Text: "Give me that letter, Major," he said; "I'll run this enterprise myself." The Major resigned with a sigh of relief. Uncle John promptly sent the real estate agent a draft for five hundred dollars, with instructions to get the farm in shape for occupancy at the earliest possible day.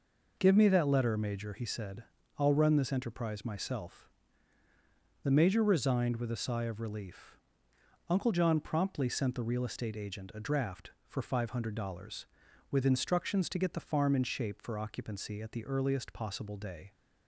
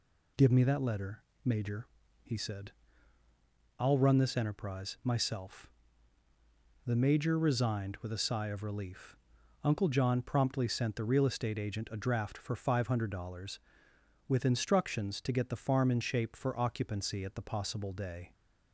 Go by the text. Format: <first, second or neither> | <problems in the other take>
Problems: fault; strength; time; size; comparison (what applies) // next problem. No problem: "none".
first | skips "earliest"; at 17.4 s